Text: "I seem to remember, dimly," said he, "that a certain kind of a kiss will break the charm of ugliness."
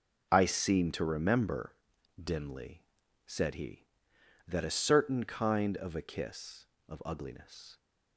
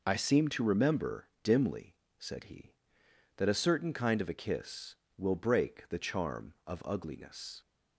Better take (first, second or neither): second